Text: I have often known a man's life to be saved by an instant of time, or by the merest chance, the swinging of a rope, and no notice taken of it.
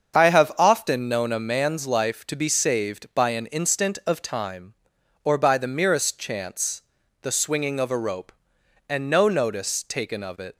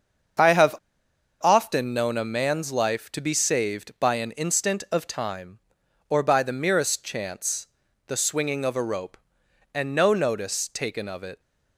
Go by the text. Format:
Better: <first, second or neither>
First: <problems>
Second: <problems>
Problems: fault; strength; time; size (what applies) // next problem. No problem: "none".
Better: first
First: starts louder than the rest; until 1.2 s; 7 dB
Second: starts louder than the rest; until 2.0 s; 7 dB // pauses between "have" and "often"; noticeable; at 0.7 s; 0.65 s long